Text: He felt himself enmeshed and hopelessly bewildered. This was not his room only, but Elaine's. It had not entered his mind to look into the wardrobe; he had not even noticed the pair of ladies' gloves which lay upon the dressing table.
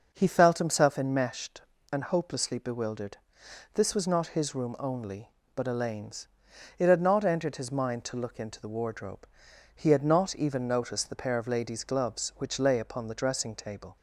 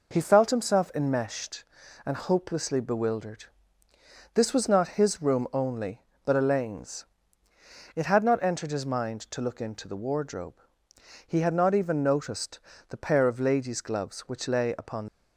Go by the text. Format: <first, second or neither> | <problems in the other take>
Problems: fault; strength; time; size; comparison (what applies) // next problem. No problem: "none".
first | pauses between "noticed" and "the"; slight; at 12.5 s; 0.30 s long // stops before "the dressing table"; at 15.0 s